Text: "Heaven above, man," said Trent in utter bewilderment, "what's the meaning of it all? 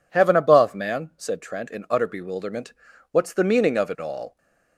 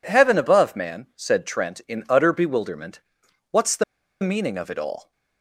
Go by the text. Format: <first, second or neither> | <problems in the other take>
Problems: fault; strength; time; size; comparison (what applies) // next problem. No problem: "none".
first | pauses between "the" and "meaning"; at 3.8 s; 0.39 s long